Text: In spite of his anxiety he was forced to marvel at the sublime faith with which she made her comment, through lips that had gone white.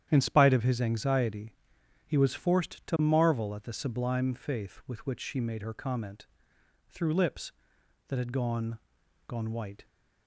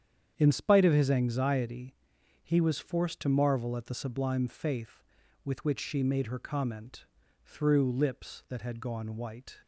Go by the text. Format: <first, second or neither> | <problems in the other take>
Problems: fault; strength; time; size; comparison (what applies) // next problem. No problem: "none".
second | starts louder than the rest; strong; until 1.1 s; 10 dB; strong in the second // pauses between "anxiety" and "he"; noticeable; at 1.5 s; 0.52 s long; noticeable in the second // says "gone" twice; at 9.2 s